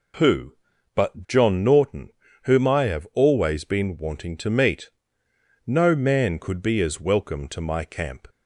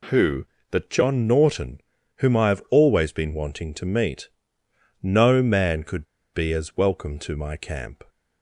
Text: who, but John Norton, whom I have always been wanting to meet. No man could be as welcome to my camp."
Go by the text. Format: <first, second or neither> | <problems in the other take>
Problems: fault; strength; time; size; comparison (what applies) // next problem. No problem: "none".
first | pauses between "could" and "be"; slight; at 6.0 s; 0.28 s long